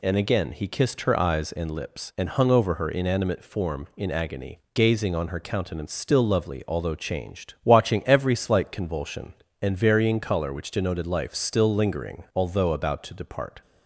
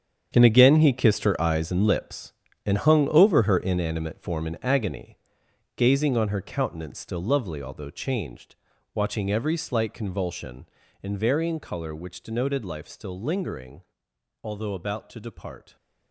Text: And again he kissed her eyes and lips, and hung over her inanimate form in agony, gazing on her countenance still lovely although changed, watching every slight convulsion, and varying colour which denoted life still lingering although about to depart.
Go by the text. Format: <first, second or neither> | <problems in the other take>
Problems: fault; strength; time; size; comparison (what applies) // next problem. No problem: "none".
first | gets quieter; strong; throughout; 12.5 dB // pauses between "lingering" and "although"; noticeable; at 13.8 s; 0.62 s long